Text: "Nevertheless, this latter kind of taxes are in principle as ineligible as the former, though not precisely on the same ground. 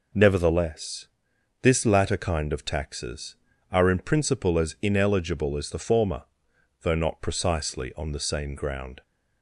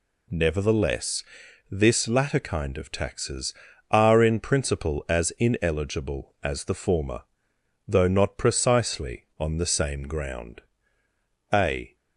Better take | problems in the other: first | goes on to say "A"; slight; from 11.5 s on; 0.42 s long

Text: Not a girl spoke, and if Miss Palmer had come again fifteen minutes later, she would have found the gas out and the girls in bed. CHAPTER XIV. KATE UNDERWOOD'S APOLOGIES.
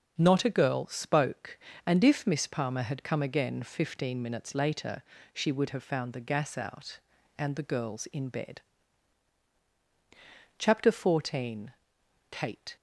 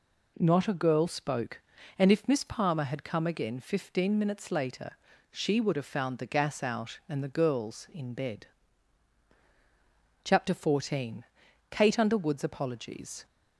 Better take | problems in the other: second | starts louder than the rest; until 1.1 s; 6 dB // stops before "UNDERWOOD'S APOLOGIES"; at 12.7 s

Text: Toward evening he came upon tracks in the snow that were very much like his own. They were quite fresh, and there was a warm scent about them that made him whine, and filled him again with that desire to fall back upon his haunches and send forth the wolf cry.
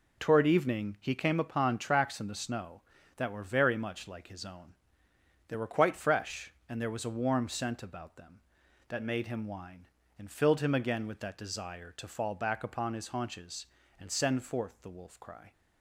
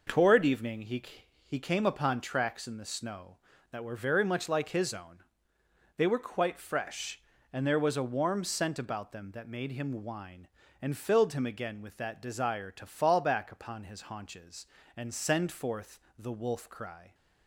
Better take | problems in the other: first | says "he" twice; at 1.4 s // pauses between "forth" and "the"; slight; at 15.9 s; 0.18 s long

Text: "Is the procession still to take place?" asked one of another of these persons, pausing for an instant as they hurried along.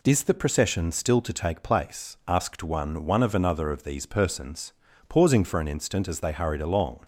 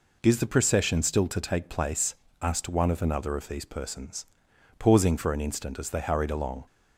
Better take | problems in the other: second | says "one" twice; at 3.0 s

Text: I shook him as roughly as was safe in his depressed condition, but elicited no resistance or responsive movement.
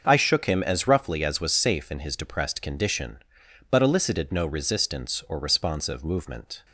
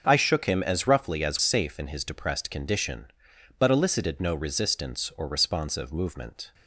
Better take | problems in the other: first | starts louder than the rest; until 1.0 s; 6.5 dB; also in the first // skips "was"; at 1.3 s

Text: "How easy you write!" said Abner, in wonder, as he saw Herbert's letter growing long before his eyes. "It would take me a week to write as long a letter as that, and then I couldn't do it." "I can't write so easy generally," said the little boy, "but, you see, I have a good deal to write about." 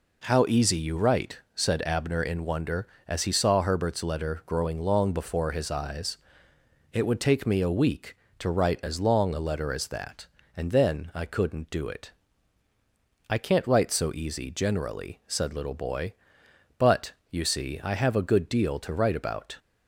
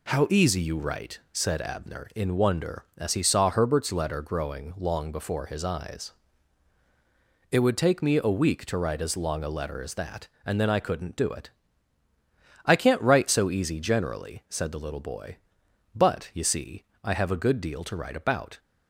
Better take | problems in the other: second | skips "the"; at 15.5 s

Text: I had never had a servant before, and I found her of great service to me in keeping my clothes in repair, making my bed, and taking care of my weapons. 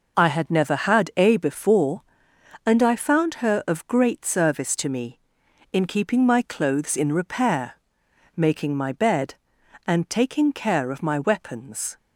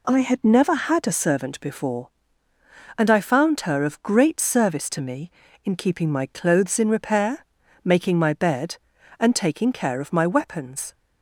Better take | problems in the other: second | skips "servant"; at 1.3 s

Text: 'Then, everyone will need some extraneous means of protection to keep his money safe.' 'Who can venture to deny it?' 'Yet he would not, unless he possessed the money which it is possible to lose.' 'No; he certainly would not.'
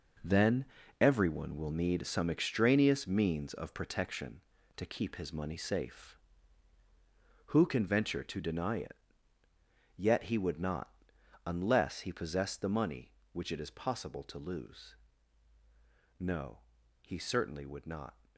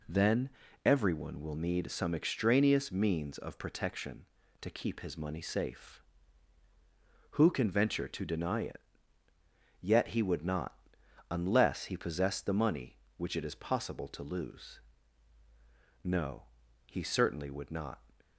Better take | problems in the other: second | gets quieter; strong; throughout; 9.5 dB

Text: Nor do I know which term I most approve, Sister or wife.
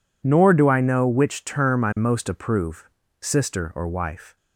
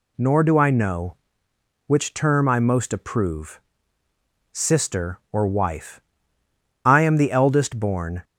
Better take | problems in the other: first | goes on to say "I am the eldest born"; from 6.8 s on; 1.3 s long

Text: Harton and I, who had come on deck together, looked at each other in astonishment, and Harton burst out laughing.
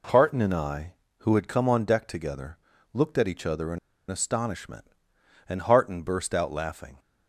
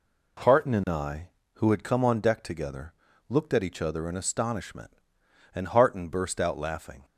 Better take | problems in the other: second | pauses between "in" and "astonishment"; slight; at 3.7 s; 0.32 s long

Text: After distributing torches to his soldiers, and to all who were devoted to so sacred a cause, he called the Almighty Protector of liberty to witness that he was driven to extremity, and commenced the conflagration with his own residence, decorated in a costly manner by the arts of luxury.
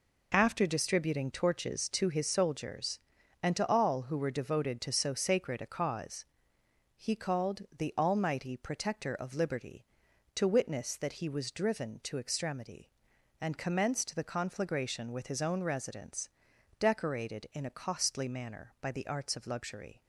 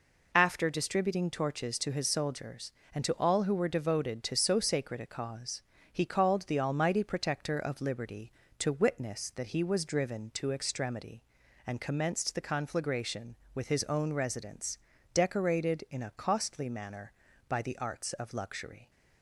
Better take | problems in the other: neither | none

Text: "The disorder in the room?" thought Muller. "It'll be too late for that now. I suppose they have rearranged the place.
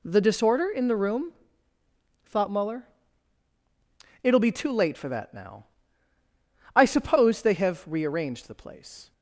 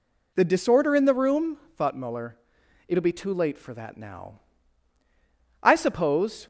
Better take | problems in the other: first | stops before "they have rearranged the place"; at 6.4 s

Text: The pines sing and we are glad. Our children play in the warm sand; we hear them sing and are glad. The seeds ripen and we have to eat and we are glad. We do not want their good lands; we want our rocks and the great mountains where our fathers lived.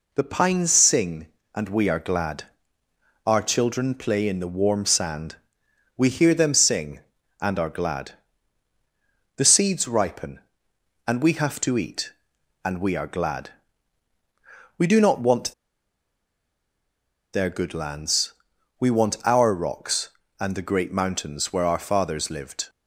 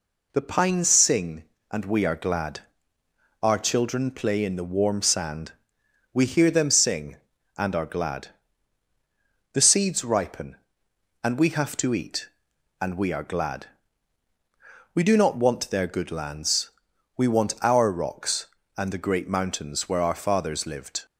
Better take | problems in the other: second | pauses between "want" and "their"; strong; at 15.5 s; 1.7 s long

